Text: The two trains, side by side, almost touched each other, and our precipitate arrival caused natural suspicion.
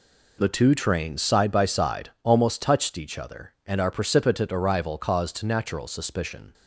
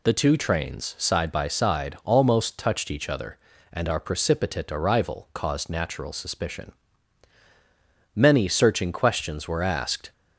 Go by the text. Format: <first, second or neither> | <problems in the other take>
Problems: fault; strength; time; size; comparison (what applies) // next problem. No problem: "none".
first | goes on to say "Many searching questions were asked"; strong; from 8.1 s on; 1.9 s long